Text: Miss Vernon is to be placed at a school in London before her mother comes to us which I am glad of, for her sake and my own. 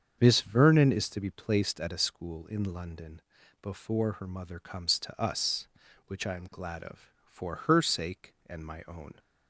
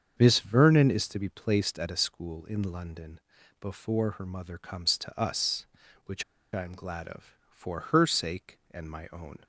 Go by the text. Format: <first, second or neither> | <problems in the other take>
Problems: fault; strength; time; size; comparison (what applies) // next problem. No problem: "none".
first | starts louder than the rest; strong; until 1.2 s; 7 dB; strong in the first // pauses between "London" and "before"; at 3.1 s; 0.42 s long; also in the first // pauses between "which" and "I"; slight; at 6.2 s; 0.30 s long